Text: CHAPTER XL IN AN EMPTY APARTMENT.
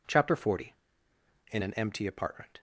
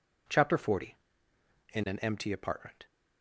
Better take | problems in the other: neither | none

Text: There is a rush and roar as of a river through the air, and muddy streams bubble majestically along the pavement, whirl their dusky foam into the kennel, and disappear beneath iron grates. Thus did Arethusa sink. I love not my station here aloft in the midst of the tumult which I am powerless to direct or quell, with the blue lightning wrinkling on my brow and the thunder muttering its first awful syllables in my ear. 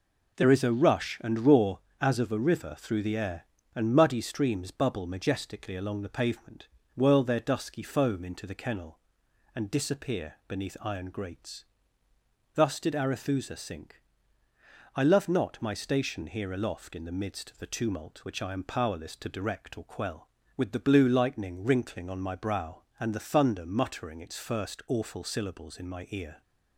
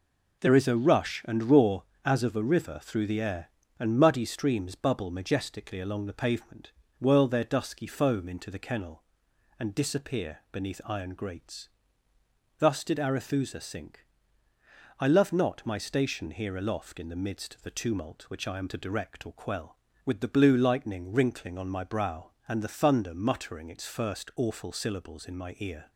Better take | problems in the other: first | skips "powerless"; at 18.6 s

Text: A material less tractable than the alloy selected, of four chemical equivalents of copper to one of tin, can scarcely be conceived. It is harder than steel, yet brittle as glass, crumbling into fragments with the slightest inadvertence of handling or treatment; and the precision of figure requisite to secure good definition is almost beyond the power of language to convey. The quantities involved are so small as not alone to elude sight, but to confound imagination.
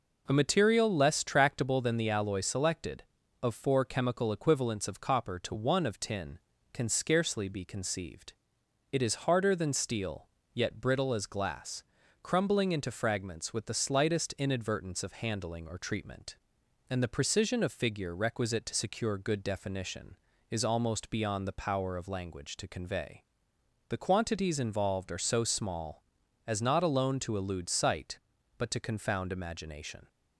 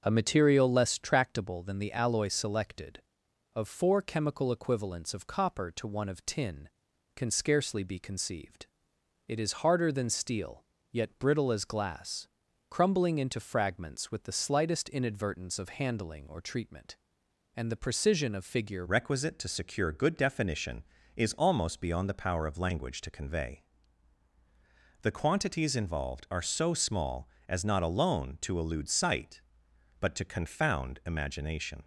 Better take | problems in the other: first | changes voice at "requisite"; from 18.8 s on; 13.0 s long

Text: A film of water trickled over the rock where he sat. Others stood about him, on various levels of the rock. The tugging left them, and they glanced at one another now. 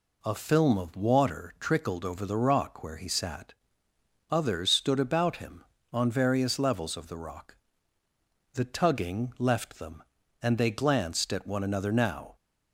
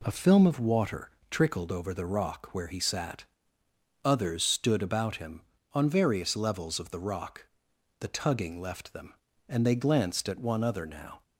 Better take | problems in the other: first | pauses between "water" and "trickled"; slight; at 1.1 s; 0.20 s long // says "other" for "another"; at 10.6 s

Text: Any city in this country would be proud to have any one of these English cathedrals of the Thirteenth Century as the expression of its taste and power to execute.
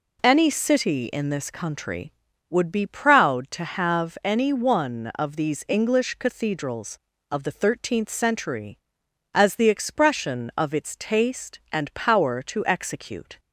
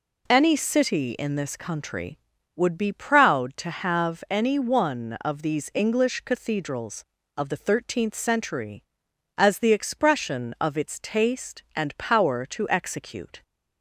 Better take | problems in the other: neither | none

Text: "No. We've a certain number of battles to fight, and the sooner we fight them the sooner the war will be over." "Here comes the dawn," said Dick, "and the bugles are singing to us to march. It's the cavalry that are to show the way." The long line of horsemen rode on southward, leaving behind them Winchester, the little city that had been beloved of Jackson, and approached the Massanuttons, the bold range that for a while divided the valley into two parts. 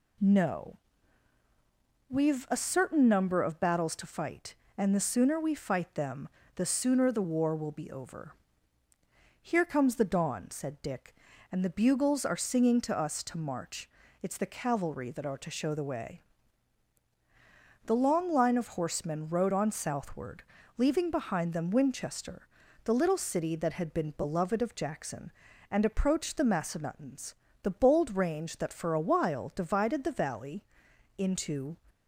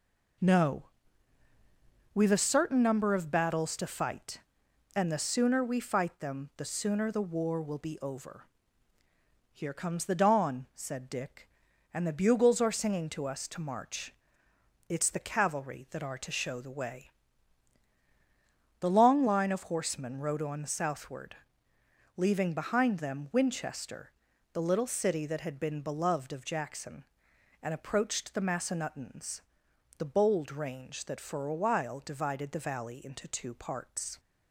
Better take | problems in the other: second | pauses between "them" and "the"; slight; at 6.2 s; 0.28 s long // pauses between "valley" and "into"; noticeable; at 30.6 s; 0.54 s long // stops before "two parts"; at 31.8 s

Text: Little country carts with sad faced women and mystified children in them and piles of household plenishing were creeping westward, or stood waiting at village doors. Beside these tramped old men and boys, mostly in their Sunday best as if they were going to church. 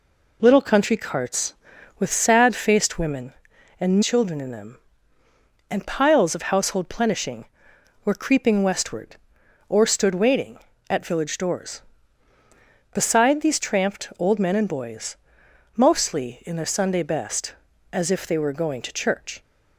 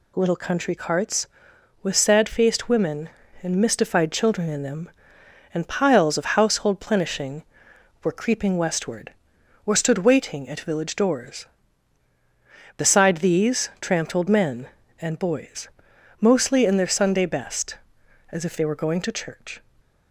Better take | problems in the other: second | skips "mystified"; at 4.0 s

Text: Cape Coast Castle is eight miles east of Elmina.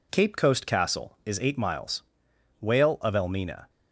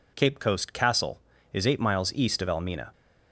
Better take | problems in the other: second | says "whale" for "east"; at 2.6 s

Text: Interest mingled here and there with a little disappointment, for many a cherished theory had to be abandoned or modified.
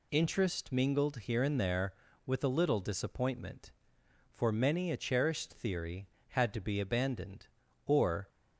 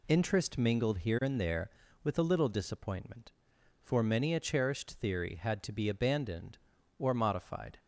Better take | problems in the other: second | stops before "modified"; at 8.2 s

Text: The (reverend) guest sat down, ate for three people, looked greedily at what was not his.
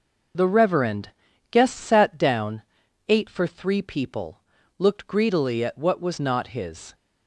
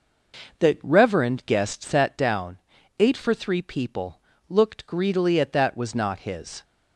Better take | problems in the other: first | says "that" for "what"; at 5.5 s

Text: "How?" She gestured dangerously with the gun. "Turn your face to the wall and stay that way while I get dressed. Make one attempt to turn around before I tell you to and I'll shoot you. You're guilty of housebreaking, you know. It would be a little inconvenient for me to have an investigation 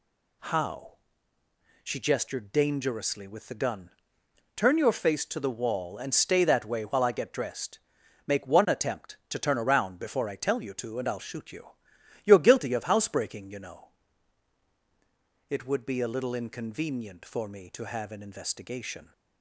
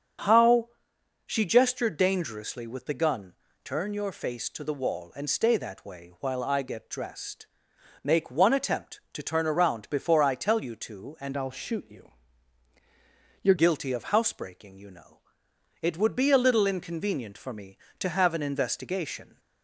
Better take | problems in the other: first | starts louder than the rest; until 1.8 s; 7 dB // changes voice from "I'll" to "You're"; from 11.3 to 13.5 s; 2.2 s long

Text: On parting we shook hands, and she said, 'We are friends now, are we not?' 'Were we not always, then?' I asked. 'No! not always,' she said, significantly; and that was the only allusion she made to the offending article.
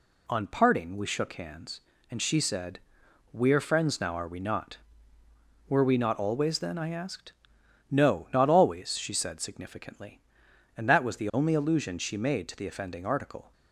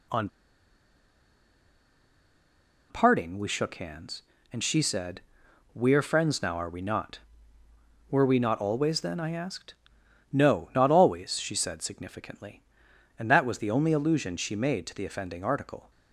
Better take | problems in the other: first | pauses between "On" and "parting"; strong; at 0.2 s; 2.6 s long

